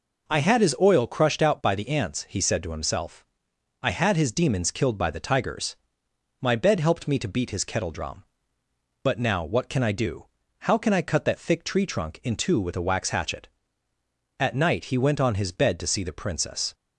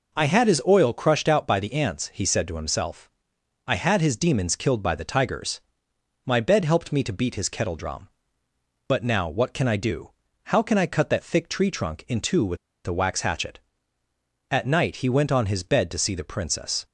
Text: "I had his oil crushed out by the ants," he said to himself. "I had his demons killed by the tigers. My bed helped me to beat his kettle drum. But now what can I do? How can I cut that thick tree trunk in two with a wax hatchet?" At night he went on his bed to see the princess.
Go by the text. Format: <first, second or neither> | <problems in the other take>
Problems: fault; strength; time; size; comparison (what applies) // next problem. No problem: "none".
first | pauses between "with" and "a"; slight; at 12.5 s; 0.29 s long